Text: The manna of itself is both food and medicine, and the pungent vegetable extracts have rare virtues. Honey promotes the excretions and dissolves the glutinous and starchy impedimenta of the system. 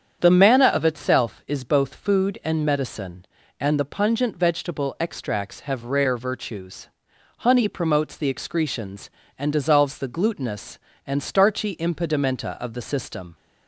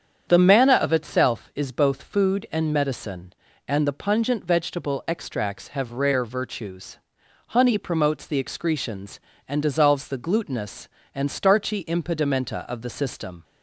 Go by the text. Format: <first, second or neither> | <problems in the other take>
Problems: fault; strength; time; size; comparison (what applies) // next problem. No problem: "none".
neither | starts louder than the rest; strong; the same in both